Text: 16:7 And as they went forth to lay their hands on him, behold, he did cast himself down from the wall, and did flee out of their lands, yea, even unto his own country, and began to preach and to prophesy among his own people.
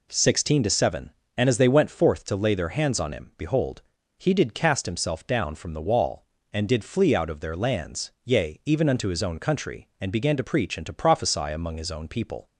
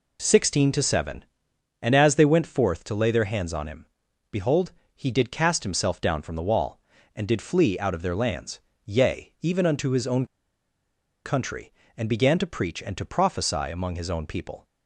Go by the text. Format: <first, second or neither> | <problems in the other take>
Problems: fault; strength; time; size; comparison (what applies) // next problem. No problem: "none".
first | pauses between "own" and "country"; at 10.2 s; 0.98 s long